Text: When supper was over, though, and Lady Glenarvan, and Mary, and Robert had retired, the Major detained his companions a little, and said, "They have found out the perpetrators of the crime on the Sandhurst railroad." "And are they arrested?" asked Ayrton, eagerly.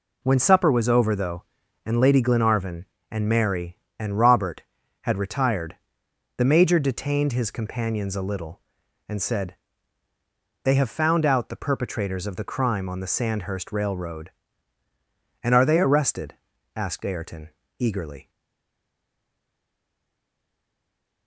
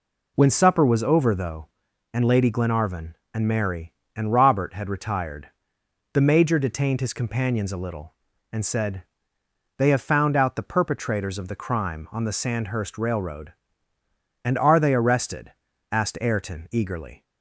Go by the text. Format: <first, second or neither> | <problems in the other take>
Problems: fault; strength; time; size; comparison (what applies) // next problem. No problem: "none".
second | stays silent after the last word; strong; from 18.2 s on; 3.0 s long